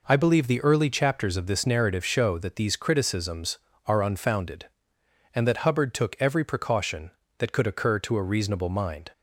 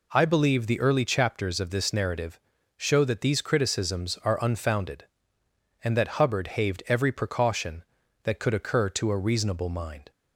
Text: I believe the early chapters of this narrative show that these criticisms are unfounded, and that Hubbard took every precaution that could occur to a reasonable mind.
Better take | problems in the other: first | pauses between "narrative" and "show"; at 2.3 s; 0.38 s long // says "haved" for "took"; at 6.4 s

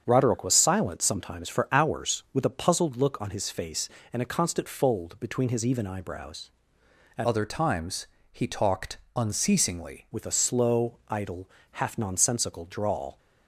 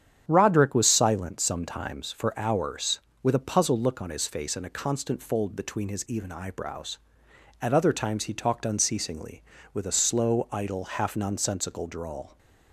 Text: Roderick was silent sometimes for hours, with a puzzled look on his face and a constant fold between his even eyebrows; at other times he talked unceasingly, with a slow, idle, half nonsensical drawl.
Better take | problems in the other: second | starts louder than the rest; strong; until 1.0 s; 7.5 dB; strong in the second // changes voice from "other" to "unceasingly"; from 7.2 to 10.0 s; 2.8 s long // pauses between "times" and "he"; slight; at 8.0 s; 0.26 s long // pauses between "talked" and "unceasingly"; slight; at 8.9 s; 0.18 s long

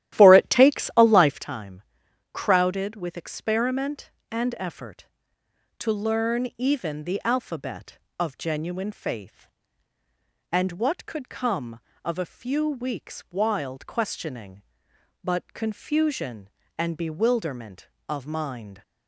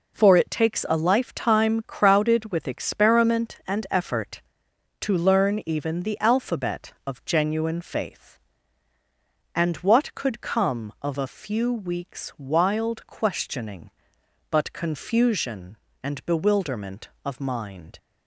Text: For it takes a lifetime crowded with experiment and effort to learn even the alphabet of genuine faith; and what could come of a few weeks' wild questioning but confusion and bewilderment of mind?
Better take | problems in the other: second | starts louder than the rest; strong; until 1.5 s; 12.5 dB // pauses between "lifetime" and "crowded"; noticeable; at 1.7 s; 0.54 s long

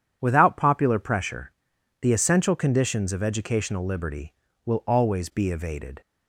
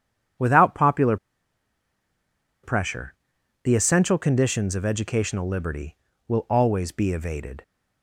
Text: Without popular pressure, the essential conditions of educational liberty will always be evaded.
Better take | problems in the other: first | pauses between "popular" and "pressure"; strong; at 1.1 s; 1.4 s long

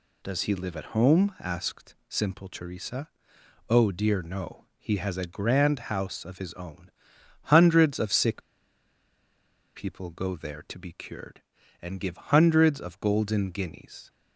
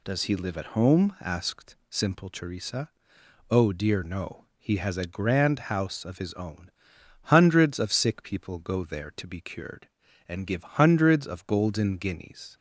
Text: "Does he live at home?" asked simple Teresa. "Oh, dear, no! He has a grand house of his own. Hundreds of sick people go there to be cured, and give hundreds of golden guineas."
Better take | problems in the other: second | pauses between "sick" and "people"; strong; at 8.4 s; 1.3 s long

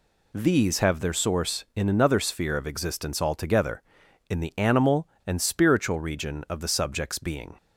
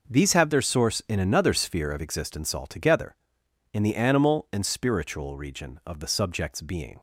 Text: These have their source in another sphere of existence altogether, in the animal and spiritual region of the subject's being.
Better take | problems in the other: neither | none

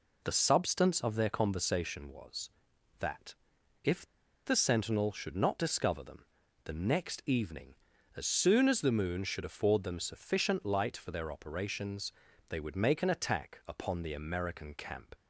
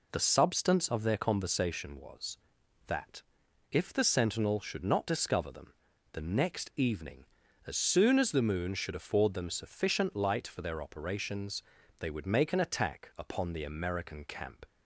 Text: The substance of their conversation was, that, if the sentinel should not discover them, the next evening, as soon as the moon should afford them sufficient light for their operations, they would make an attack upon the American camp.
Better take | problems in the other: second | pauses between "if" and "the"; at 4.0 s; 0.39 s long

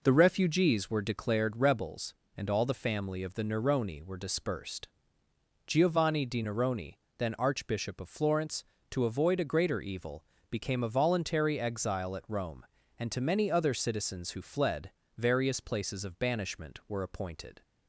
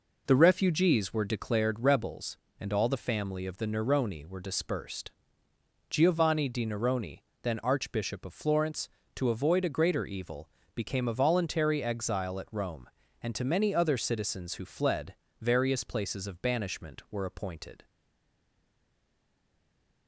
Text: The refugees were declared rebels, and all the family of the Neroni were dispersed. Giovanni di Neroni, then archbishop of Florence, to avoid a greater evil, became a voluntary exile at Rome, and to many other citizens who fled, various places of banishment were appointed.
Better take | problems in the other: first | stays silent after the last word; from 17.8 s on; 2.2 s long

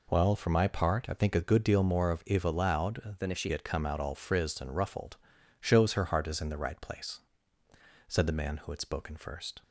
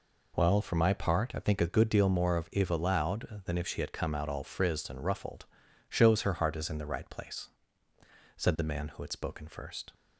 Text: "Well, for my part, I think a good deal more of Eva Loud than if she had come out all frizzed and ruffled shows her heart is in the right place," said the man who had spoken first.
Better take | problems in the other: second | changes voice from "than" to "she"; from 3.1 to 3.5 s; 0.4 s long // pauses between "ruffled" and "shows"; at 5.1 s; 0.44 s long; also in the second

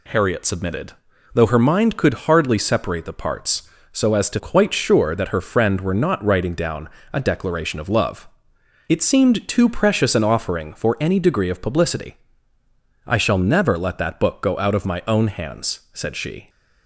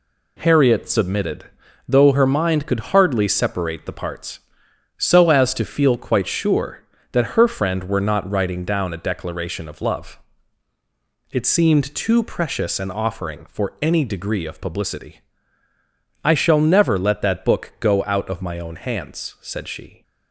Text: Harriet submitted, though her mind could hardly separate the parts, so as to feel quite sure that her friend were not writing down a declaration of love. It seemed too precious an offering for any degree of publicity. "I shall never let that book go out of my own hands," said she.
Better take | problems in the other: second | skips "feel"; at 4.3 s // pauses between "down" and "a"; slight; at 6.8 s; 0.24 s long

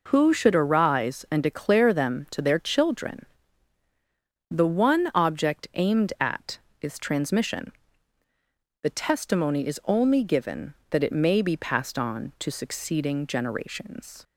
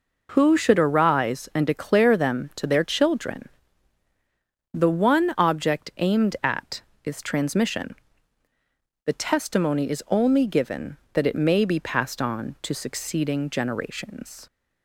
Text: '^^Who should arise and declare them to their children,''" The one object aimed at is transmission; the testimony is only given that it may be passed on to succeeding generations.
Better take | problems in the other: neither | none

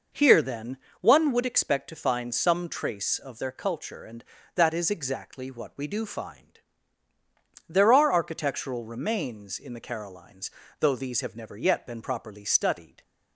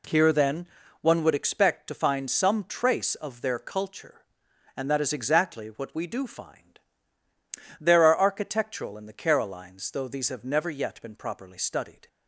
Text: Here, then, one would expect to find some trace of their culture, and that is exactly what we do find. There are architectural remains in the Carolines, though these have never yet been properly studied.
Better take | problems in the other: first | skips "remains"; at 8.9 s

